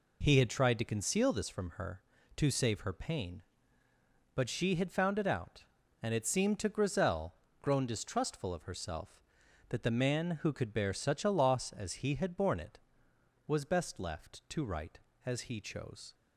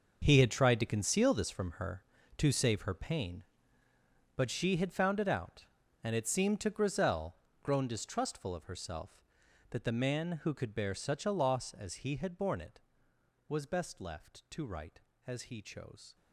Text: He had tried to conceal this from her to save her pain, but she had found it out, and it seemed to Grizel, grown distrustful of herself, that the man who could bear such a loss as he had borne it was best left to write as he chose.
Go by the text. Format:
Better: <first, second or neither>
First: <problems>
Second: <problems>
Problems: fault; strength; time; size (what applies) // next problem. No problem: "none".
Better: first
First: none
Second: gets quieter; strong; throughout; 14 dB